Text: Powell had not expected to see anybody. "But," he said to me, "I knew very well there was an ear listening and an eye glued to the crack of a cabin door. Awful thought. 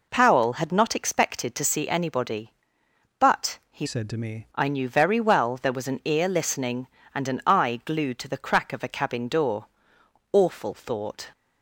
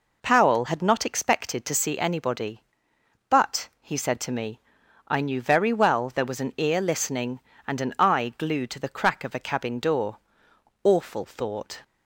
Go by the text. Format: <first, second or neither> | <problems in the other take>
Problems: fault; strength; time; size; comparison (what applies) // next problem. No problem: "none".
second | changes voice from "said" to "me"; from 3.8 to 4.4 s; 0.6 s long